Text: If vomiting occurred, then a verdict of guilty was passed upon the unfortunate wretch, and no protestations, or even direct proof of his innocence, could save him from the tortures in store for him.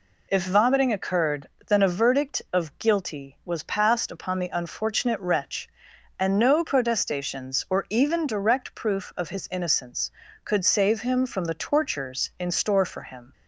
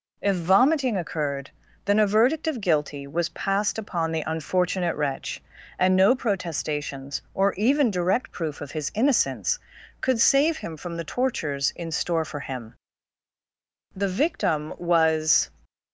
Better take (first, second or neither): first